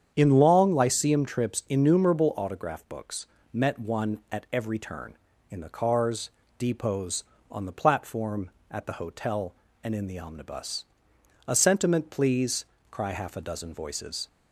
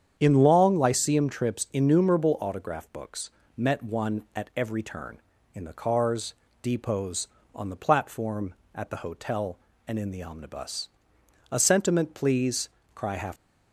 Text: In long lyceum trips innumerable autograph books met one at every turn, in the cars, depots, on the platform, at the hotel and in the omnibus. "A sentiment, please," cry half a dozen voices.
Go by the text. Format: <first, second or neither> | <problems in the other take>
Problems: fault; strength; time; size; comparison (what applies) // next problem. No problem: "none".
first | starts louder than the rest; strong; until 1.1 s; 8.5 dB; strong in the first // pauses between "books" and "met"; slight; at 3.2 s; 0.26 s long; slight in the first // stops before "a dozen voices"; at 13.3 s